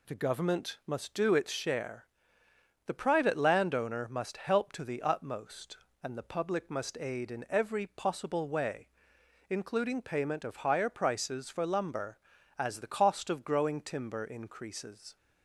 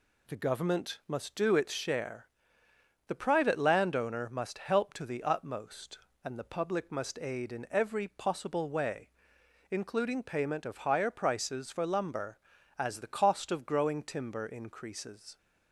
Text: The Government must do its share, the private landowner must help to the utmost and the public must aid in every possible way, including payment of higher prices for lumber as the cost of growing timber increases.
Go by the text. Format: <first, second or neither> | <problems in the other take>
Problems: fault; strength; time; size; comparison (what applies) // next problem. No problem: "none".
neither | none